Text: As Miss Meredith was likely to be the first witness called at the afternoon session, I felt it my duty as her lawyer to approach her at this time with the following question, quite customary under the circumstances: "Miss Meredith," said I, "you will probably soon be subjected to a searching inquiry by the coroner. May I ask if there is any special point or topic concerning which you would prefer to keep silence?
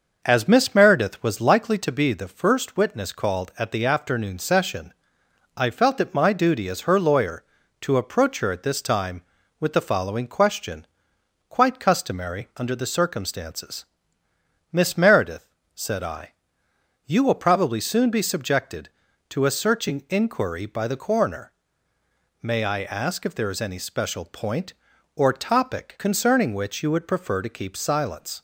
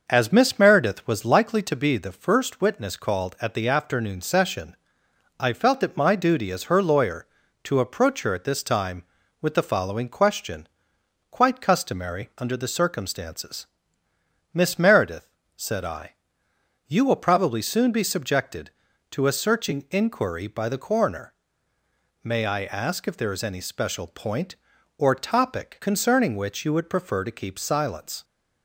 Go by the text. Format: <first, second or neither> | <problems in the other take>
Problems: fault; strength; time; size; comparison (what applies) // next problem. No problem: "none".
neither | none